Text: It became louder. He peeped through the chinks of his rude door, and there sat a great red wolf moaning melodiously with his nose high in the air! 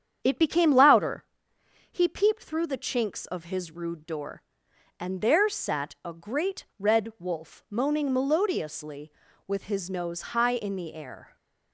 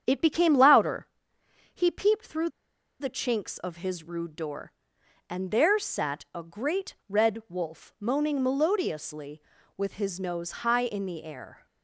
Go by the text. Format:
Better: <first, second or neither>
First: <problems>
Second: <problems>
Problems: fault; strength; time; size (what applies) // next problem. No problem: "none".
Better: first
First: starts louder than the rest; strong; until 1.2 s; 8.5 dB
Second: starts louder than the rest; strong; until 1.0 s; 8.5 dB // pauses between "through" and "the"; noticeable; at 2.4 s; 0.50 s long